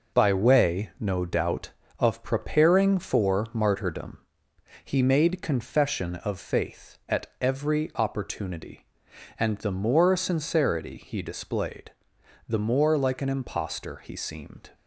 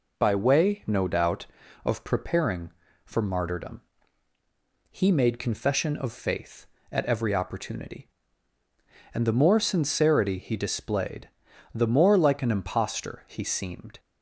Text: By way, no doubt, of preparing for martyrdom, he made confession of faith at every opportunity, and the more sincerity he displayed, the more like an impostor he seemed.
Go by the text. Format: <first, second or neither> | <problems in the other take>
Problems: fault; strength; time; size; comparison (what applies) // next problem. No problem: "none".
second | gets quieter; throughout; 6.5 dB // pauses between "at" and "every"; slight; at 7.2 s; 0.16 s long